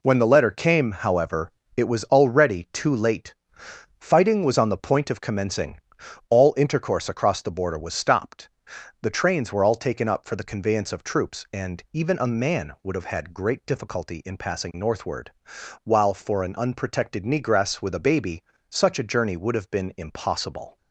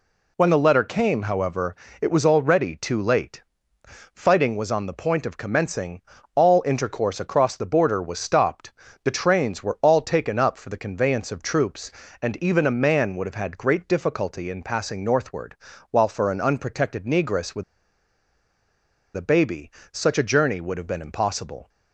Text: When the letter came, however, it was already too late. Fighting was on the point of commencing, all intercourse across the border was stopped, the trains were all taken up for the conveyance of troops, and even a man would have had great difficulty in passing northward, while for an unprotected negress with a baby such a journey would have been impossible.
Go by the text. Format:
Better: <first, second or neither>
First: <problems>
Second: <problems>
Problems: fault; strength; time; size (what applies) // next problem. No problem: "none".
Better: first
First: pauses between "baby" and "such"; slight; at 18.4 s; 0.26 s long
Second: pauses between "with" and "a"; strong; at 17.6 s; 1.5 s long // pauses between "baby" and "such"; slight; at 19.6 s; 0.24 s long